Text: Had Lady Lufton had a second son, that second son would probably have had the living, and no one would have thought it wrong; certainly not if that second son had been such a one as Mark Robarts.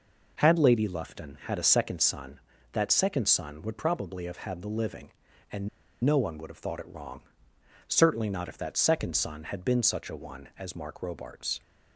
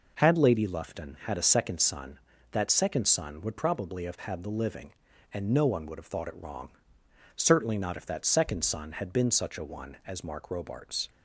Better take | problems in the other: second | pauses between "and" and "no"; slight; at 5.6 s; 0.36 s long

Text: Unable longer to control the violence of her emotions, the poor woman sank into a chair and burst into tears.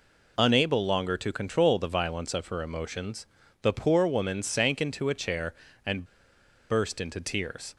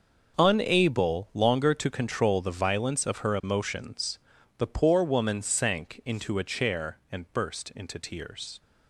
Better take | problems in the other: second | pauses between "and" and "burst"; noticeable; at 6.0 s; 0.66 s long

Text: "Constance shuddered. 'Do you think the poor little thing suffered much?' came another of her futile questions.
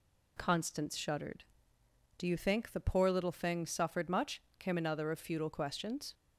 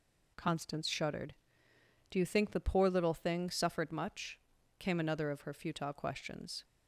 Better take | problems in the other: second | skips "her"; at 5.1 s

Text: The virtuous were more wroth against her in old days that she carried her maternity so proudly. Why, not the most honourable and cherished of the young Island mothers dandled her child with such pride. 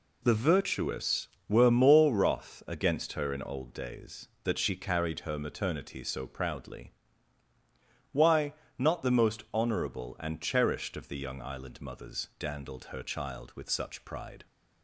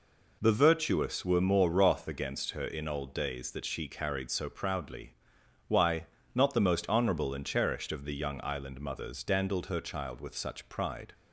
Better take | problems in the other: first | skips "her maternity"; at 4.3 s

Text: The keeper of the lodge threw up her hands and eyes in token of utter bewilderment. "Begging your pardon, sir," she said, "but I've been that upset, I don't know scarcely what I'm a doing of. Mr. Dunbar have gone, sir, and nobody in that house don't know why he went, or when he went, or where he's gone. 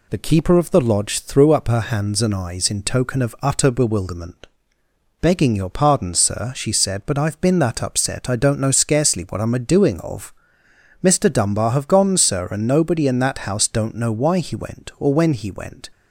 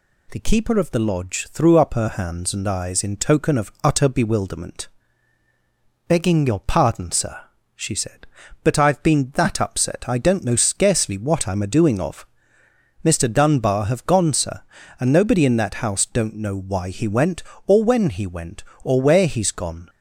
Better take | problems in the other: second | stops before "or where he's gone"; at 15.9 s

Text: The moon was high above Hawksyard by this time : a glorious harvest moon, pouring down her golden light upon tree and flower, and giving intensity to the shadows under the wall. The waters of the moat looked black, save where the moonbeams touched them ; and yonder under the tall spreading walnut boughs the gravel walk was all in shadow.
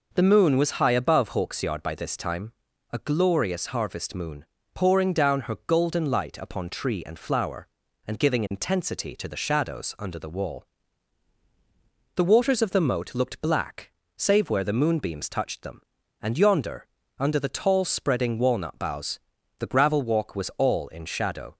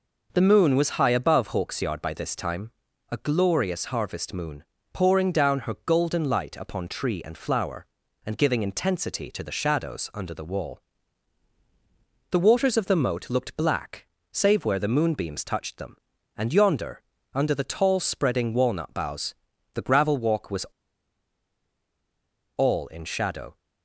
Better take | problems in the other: first | pauses between "yonder" and "under"; slight; at 17.0 s; 0.32 s long; slight in the first // pauses between "boughs" and "the"; at 19.3 s; 0.38 s long; also in the first // pauses between "was" and "all"; strong; at 20.6 s; 1.9 s long

